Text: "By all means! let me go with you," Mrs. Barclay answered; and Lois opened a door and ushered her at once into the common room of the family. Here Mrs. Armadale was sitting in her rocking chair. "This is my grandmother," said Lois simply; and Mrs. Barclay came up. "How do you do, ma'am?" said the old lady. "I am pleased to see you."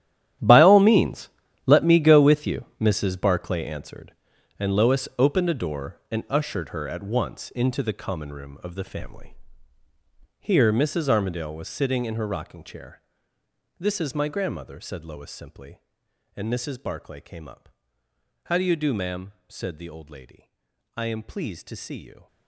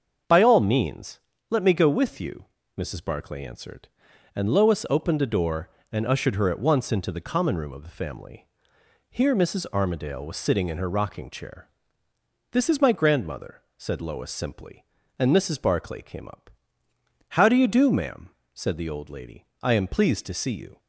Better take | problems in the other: second | gets quieter; strong; throughout; 15 dB // starts louder than the rest; strong; until 1.7 s; 12 dB; also in the second

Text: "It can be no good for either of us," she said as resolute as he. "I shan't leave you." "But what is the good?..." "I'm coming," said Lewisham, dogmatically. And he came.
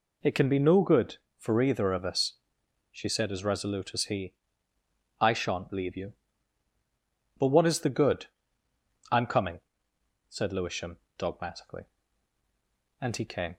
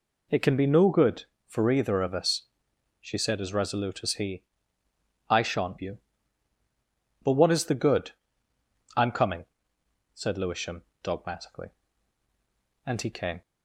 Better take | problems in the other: first | skips "leave"; at 5.7 s

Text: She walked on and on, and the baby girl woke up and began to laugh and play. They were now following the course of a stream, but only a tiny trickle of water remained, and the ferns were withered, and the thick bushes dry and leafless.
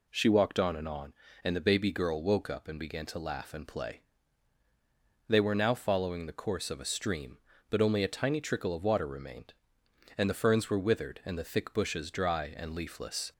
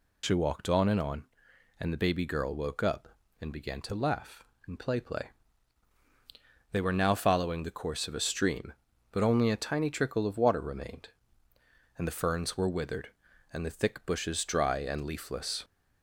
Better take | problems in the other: first | says "play" twice; at 4.9 s

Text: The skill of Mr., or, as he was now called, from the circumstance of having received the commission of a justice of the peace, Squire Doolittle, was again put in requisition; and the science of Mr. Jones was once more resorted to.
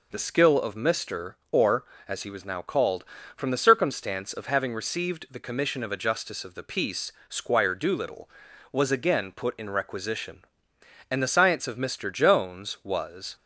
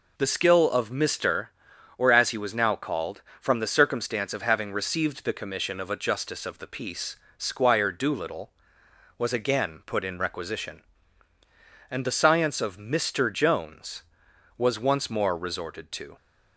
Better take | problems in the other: second | stops before "once more resorted to"; at 13.3 s

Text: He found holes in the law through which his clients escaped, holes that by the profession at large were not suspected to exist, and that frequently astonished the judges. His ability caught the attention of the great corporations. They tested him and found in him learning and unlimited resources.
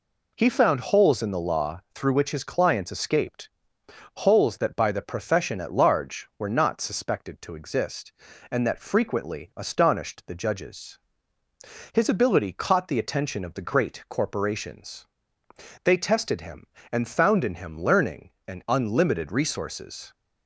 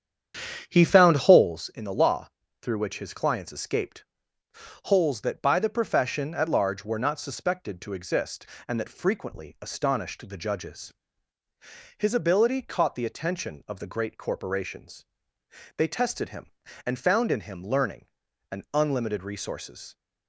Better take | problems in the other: first | starts louder than the rest; strong; until 1.6 s; 8.5 dB // pauses between "law" and "through"; slight; at 2.2 s; 0.32 s long

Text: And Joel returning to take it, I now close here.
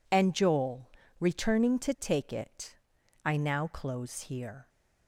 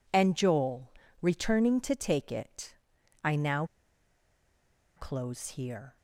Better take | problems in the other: first | pauses between "Joel" and "returning"; slight; at 0.8 s; 0.30 s long; slight in the first // pauses between "now" and "close"; strong; at 3.6 s; 1.3 s long

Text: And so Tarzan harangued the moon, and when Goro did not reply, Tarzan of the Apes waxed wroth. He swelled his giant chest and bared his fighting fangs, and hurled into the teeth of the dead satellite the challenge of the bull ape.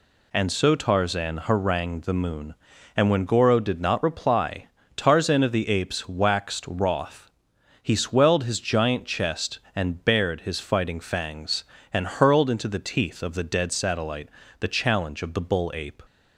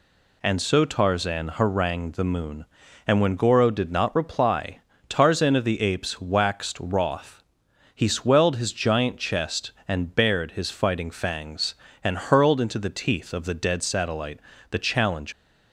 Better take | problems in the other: first | pauses between "satellite" and "the"; slight; at 14.3 s; 0.32 s long; slight in the first // stops before "of the bull ape"; at 15.3 s

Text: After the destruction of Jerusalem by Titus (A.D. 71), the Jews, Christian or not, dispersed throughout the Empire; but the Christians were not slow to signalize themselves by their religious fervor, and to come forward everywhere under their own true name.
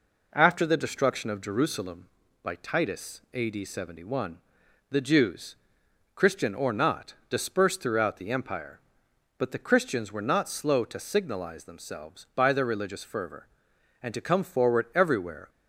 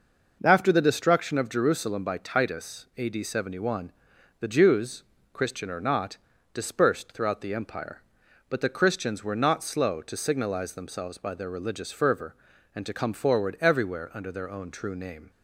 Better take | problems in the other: second | stops before "under their own true name"; at 15.4 s

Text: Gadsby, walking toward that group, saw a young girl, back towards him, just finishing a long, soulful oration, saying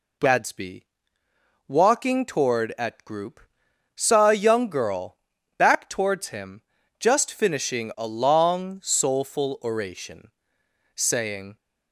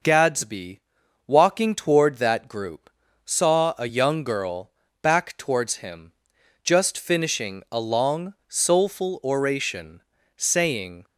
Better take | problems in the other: second | says "at" for "that"; at 2.7 s

